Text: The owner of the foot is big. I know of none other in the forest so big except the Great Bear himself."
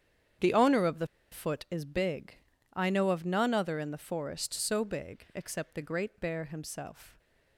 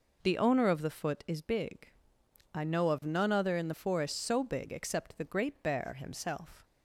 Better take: second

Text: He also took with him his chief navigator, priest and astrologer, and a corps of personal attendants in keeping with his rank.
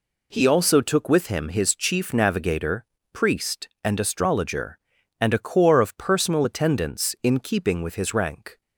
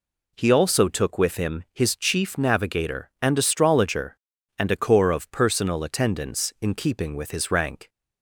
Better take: first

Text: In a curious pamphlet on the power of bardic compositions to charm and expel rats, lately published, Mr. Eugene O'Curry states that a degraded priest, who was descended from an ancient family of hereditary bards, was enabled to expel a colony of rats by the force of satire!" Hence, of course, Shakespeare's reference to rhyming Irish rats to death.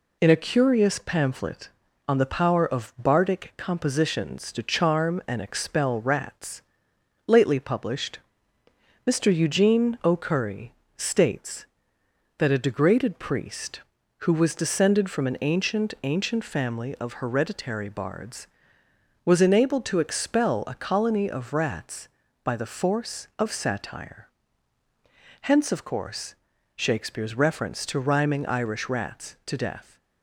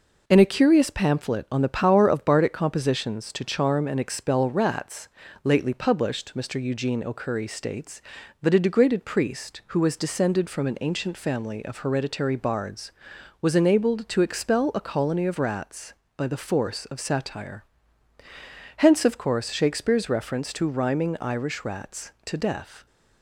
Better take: second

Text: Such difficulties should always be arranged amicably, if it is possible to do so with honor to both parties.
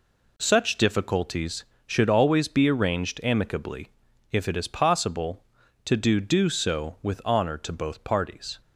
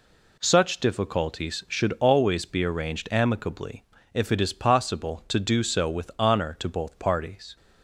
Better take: second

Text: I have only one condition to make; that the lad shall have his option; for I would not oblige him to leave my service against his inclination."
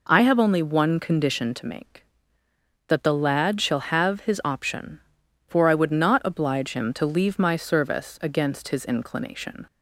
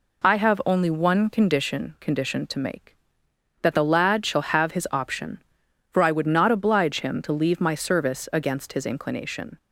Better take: first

